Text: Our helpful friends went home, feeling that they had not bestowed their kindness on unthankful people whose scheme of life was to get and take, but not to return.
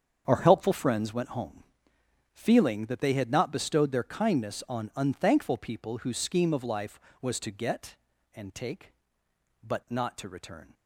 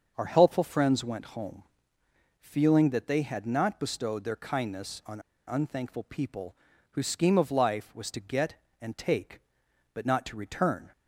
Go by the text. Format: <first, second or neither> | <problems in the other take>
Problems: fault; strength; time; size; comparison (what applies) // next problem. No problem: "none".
first | starts louder than the rest; until 1.1 s; 6.5 dB; strong in the first // pauses between "on" and "unthankful"; slight; at 5.2 s; 0.26 s long // pauses between "people" and "whose"; slight; at 6.5 s; 0.36 s long